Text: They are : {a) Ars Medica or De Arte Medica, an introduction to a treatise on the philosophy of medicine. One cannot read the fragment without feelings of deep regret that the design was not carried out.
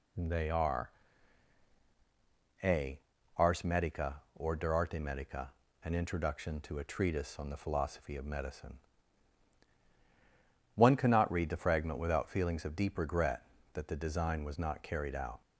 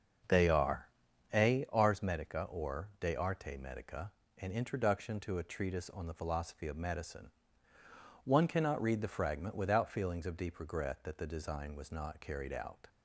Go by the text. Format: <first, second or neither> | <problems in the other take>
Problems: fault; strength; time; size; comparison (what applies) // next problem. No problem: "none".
first | starts louder than the rest; until 1.6 s; 6.5 dB